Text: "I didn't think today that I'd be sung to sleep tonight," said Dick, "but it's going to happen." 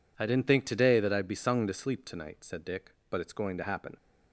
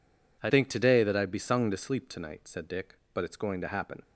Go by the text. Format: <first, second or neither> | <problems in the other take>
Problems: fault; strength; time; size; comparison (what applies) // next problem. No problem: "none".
first | skips "didn't"; at 0.5 s